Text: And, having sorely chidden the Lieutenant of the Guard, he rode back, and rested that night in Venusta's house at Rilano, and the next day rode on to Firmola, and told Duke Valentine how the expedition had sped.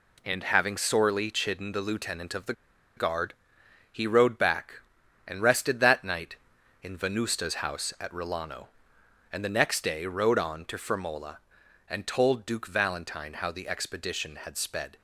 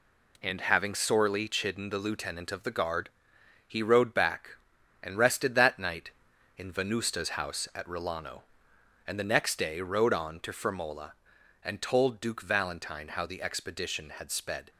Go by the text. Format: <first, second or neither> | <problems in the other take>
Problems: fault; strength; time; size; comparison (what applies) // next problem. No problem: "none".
second | pauses between "the" and "Guard"; at 2.5 s; 0.44 s long